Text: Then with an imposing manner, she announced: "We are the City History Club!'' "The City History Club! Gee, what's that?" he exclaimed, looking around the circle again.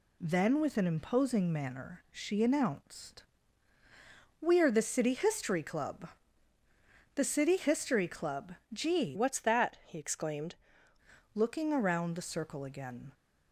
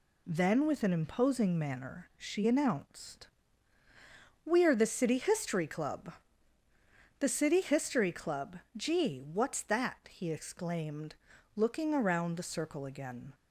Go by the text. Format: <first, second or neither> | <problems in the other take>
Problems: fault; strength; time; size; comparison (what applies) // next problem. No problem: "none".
second | changes voice from "what's" to "exclaimed"; from 9.1 to 10.5 s; 1.4 s long